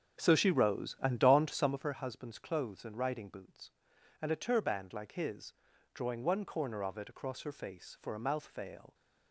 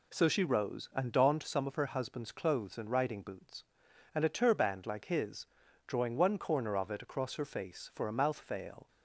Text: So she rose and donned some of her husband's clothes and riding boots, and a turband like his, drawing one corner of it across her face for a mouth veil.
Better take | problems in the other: second | starts louder than the rest; until 1.9 s; 7 dB

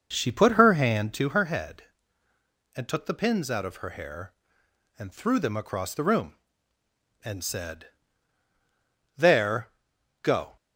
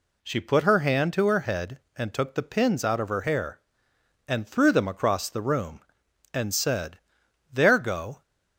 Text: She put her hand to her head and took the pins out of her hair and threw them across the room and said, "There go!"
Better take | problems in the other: second | starts louder than the rest; noticeable; until 1.3 s; 6 dB // pauses between "There" and "go"; noticeable; at 9.6 s; 0.54 s long

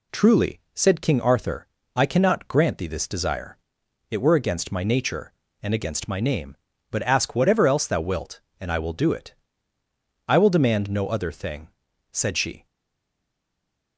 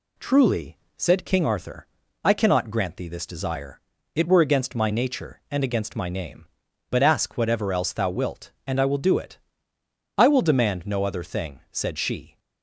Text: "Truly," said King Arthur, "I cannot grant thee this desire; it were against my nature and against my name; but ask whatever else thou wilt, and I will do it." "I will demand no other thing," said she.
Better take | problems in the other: second | stays silent after the last word; noticeable; from 12.6 s on; 1.3 s long

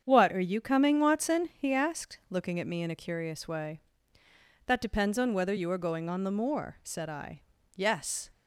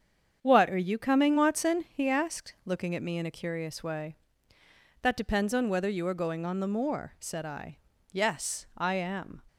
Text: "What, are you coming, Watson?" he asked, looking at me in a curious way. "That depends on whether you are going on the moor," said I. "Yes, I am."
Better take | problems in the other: second | starts louder than the rest; strong; until 1.0 s; 7.5 dB; strong in the second // stops before "I am"; at 8.3 s

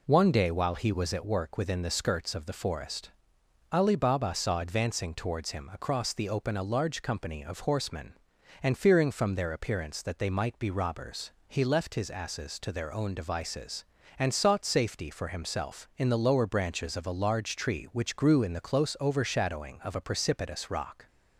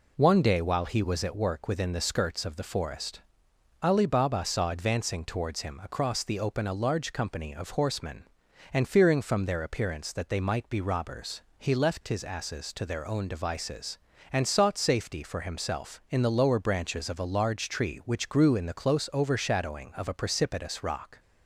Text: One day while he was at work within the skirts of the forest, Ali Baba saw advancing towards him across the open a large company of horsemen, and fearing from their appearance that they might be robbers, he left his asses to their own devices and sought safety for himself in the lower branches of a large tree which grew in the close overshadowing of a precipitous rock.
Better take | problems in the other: neither | none

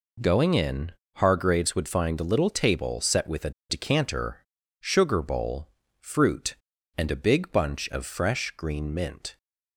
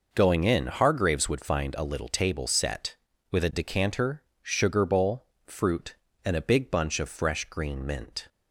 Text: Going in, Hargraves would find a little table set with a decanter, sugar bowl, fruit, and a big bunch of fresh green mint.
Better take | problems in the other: second | pauses between "a" and "decanter"; slight; at 3.5 s; 0.19 s long

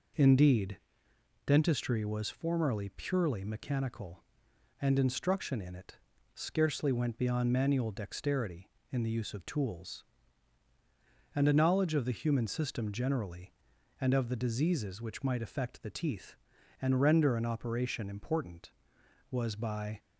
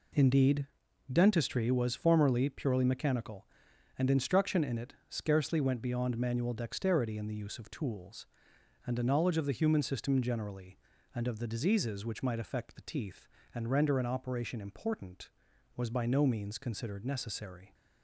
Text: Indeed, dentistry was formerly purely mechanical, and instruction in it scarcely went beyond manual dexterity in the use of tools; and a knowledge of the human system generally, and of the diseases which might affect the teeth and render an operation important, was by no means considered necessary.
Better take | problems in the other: second | pauses between "it" and "scarcely"; slight; at 5.9 s; 0.36 s long; slight in the second // stops before "no means considered necessary"; at 19.9 s

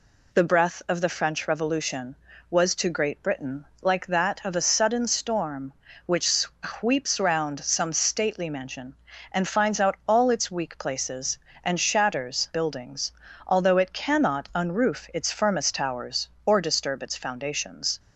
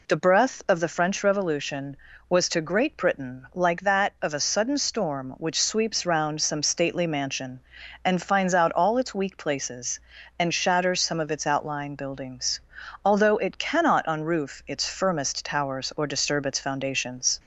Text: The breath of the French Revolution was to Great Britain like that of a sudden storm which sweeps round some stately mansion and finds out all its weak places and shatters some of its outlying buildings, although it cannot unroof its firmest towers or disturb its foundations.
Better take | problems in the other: second | pauses between "Britain" and "like"; slight; at 3.6 s; 0.16 s long // skips "some of its outlying"; at 12.5 s

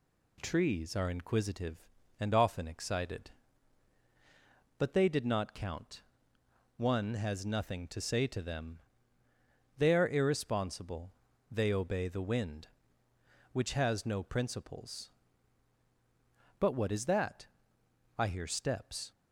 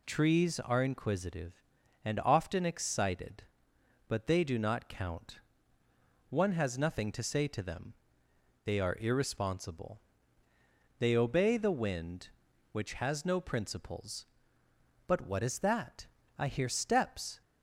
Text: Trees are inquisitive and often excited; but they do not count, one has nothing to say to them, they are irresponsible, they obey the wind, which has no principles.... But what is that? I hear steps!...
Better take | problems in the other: second | says "did" for "do"; at 5.0 s

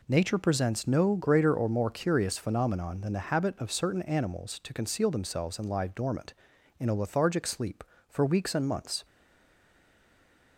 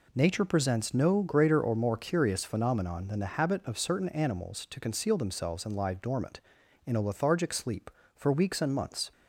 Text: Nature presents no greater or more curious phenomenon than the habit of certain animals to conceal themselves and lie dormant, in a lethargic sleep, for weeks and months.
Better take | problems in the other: second | stays silent after the last word; noticeable; from 9.0 s on; 1.5 s long

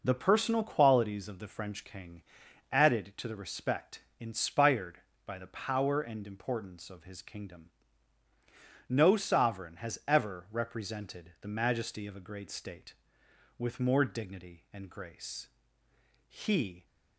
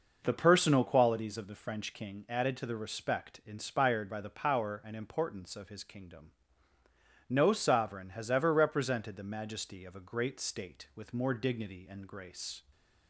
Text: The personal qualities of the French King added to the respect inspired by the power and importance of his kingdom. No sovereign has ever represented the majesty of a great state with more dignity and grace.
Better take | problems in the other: second | pauses between "King" and "added"; noticeable; at 2.2 s; 0.50 s long // pauses between "respect" and "inspired"; slight; at 4.0 s; 0.18 s long // goes on to say "He"; from 16.2 s on; 0.58 s long

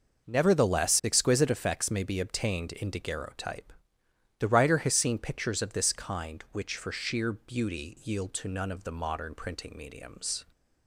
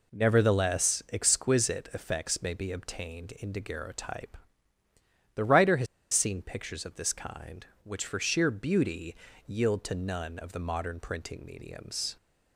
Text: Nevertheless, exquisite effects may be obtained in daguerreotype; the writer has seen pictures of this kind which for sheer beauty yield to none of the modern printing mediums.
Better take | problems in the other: first | pauses between "has" and "seen"; slight; at 5.8 s; 0.27 s long // pauses between "beauty" and "yield"; slight; at 9.1 s; 0.32 s long

